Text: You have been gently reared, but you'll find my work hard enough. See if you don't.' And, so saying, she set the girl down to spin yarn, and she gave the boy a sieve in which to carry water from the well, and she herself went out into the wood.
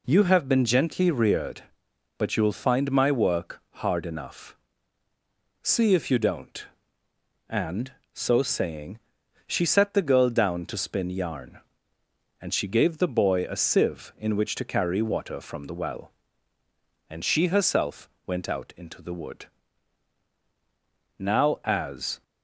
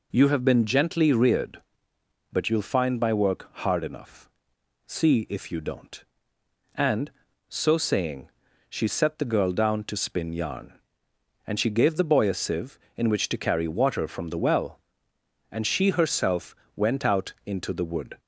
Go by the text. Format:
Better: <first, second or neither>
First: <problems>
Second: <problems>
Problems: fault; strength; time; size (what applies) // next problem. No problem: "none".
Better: second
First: pauses between "work" and "hard"; slight; at 3.6 s; 0.18 s long // pauses between "herself" and "went"; slight; at 18.0 s; 0.18 s long // goes on to say "Now as"; noticeable; from 21.1 s on; 1.0 s long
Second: pauses between "herself" and "went"; slight; at 16.5 s; 0.20 s long